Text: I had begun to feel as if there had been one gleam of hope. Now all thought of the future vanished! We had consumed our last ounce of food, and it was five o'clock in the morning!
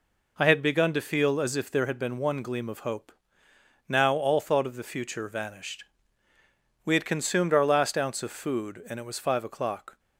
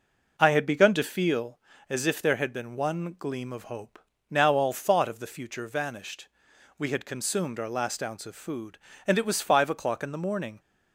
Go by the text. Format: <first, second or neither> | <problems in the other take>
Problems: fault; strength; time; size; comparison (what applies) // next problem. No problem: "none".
second | stops before "in the morning"; at 9.9 s